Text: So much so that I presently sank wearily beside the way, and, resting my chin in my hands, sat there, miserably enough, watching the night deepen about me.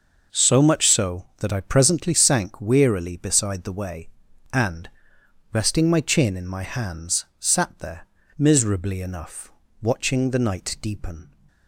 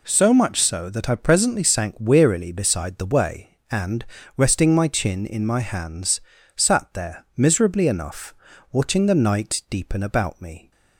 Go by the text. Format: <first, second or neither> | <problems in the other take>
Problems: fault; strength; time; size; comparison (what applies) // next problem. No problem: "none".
second | stops before "about me"; at 11.4 s